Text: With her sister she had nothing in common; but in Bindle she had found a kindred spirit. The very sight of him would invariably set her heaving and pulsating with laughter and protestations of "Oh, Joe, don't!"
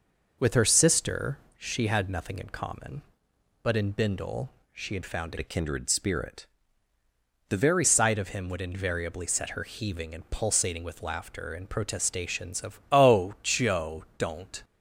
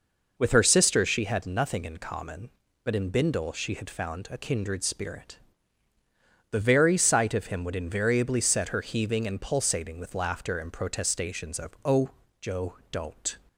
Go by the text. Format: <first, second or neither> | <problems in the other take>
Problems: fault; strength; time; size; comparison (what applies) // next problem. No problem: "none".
second | pauses between "sister" and "she"; slight; at 1.3 s; 0.20 s long // pauses between "Bindle" and "she"; slight; at 4.5 s; 0.20 s long // changes voice from "a" to "very"; from 5.3 to 7.8 s; 2.5 s long